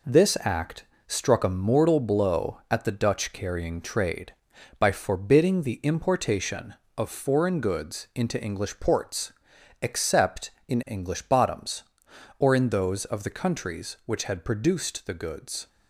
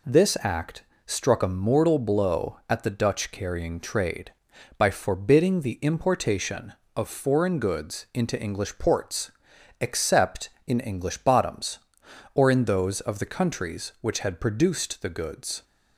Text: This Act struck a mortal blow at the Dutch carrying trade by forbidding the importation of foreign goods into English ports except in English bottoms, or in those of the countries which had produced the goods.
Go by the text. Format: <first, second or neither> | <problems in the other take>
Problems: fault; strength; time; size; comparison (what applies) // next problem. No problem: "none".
second | gets quieter; noticeable; throughout; 5.5 dB // pauses between "Act" and "struck"; slight; at 0.8 s; 0.22 s long; slight in the second // pauses between "ports" and "except"; noticeable; at 9.3 s; 0.48 s long; noticeable in the second